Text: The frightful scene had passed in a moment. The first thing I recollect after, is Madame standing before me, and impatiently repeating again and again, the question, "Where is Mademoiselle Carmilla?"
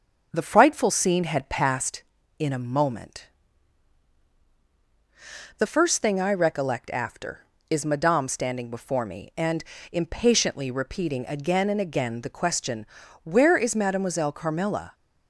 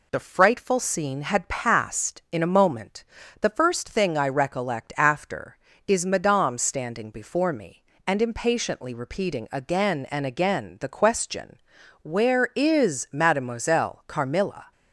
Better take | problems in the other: second | starts louder than the rest; until 2.0 s; 6 dB // pauses between "and" and "impatiently"; slight; at 9.6 s; 0.30 s long

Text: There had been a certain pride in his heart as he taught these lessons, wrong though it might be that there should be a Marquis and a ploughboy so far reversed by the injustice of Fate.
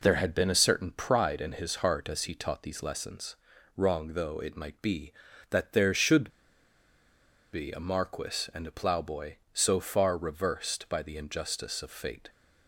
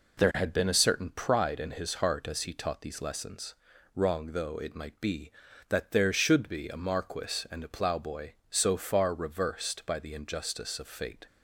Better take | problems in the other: second | pauses between "should" and "be"; at 6.2 s; 1.2 s long

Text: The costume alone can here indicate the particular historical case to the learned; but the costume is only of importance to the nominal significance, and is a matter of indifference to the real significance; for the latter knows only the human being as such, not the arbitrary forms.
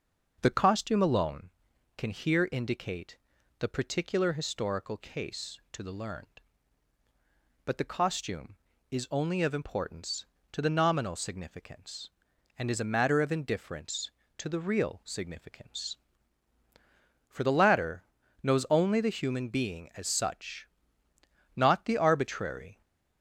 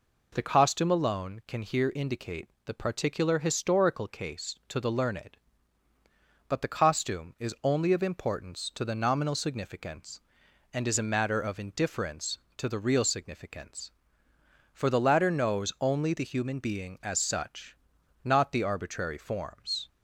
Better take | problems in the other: second | starts louder than the rest; until 1.4 s; 6 dB // pauses between "indicate" and "the"; at 3.1 s; 0.42 s long; slight in the second // pauses between "latter" and "knows"; slight; at 18.0 s; 0.36 s long // stops before "forms"; at 22.8 s

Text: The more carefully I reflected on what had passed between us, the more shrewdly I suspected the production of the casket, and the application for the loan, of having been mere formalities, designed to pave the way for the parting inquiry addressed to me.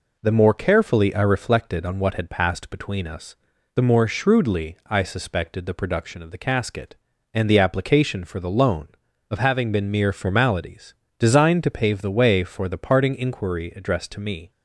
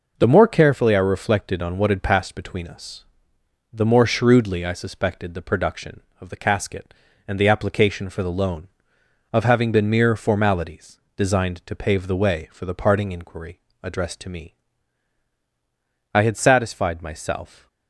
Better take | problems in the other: first | pauses between "inquiry" and "addressed"; slight; at 13.5 s; 0.24 s long // goes on to say "I had satisfied myself"; from 16.1 s on; 1.5 s long

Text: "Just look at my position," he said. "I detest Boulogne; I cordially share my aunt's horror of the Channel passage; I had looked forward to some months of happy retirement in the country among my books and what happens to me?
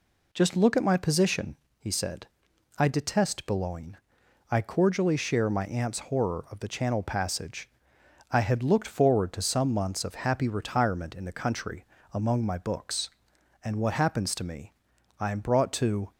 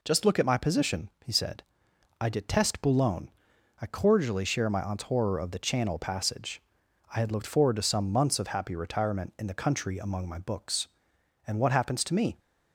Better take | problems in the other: second | pauses between "country" and "among"; slight; at 11.8 s; 0.30 s long // goes on to say "I am brought to"; noticeable; from 15.1 s on; 0.92 s long

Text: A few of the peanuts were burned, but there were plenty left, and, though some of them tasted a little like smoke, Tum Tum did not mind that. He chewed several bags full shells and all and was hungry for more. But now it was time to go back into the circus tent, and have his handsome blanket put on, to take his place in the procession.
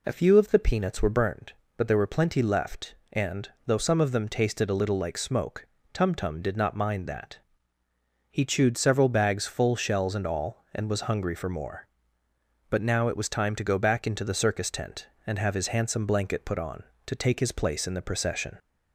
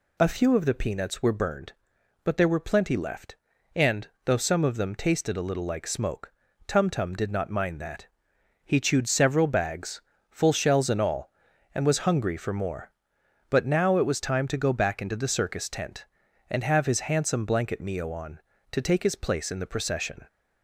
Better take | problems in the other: first | pauses between "bags" and "full"; slight; at 10.0 s; 0.30 s long // says "mio" for "put"; at 17.8 s

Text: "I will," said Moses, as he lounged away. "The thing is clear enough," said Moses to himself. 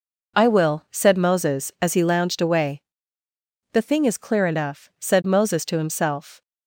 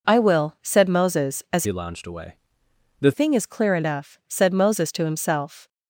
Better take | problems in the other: first | changes voice from "he" to "The"; from 1.6 to 3.1 s; 1.5 s long

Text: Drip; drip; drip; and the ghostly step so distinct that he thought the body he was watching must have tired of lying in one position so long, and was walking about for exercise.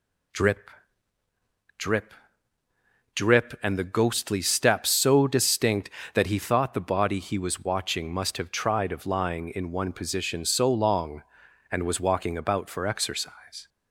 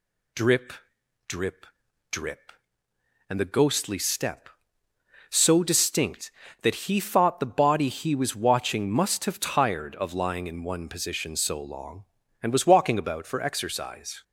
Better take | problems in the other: second | says "tried" for "tired"; at 8.5 s

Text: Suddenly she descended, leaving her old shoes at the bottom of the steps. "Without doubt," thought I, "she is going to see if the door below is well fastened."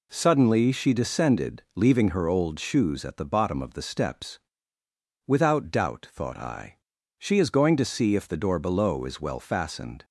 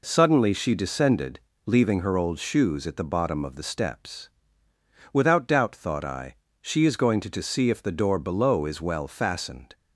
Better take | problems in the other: first | says "to" twice; at 7.3 s

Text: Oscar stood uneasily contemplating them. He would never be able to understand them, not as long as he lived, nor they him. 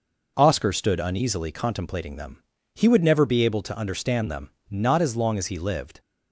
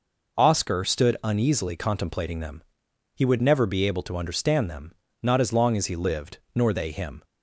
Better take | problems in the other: second | stops before "nor they him"; at 5.9 s

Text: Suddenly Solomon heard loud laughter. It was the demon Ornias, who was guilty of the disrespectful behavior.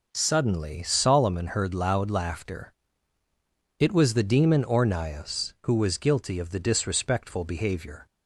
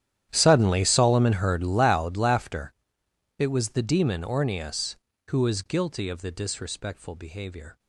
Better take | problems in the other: first | gets quieter; strong; throughout; 20.5 dB

